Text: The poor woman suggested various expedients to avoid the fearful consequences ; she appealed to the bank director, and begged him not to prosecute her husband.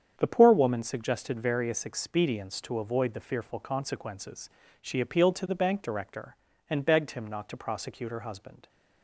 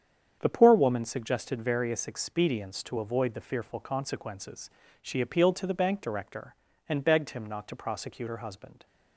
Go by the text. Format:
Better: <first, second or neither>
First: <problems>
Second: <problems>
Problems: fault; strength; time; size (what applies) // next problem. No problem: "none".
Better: neither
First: starts louder than the rest; strong; until 1.2 s; 8 dB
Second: starts louder than the rest; strong; until 1.4 s; 8 dB